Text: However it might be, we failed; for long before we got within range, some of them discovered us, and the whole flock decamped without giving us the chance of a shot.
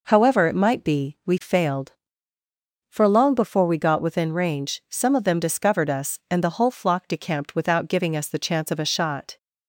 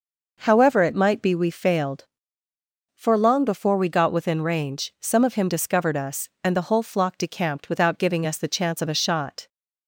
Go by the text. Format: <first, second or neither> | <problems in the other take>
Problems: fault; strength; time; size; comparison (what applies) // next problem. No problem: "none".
first | says "him" for "them"; at 5.3 s